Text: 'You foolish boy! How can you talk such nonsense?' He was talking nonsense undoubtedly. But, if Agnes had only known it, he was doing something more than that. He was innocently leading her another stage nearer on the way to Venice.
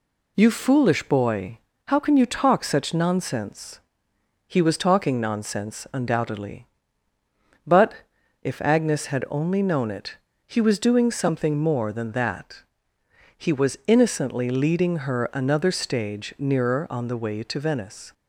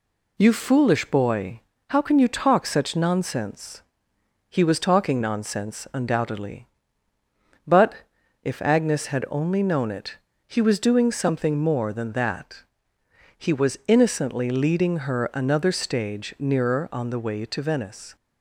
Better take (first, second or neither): neither